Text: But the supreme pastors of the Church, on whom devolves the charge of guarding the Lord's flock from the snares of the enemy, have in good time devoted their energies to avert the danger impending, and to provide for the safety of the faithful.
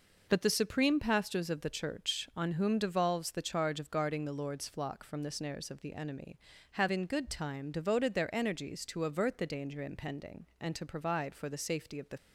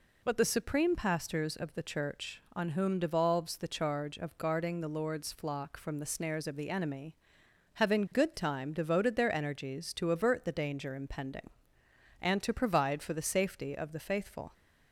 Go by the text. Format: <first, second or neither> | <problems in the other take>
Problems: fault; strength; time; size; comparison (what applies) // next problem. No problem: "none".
second | stops before "faithful"; at 12.1 s